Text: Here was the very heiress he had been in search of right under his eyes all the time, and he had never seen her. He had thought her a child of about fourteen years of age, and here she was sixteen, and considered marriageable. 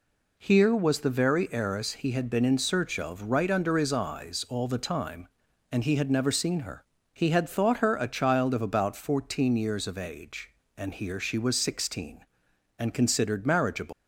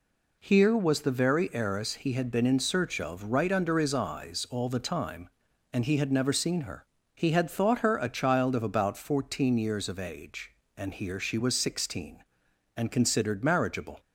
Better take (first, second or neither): second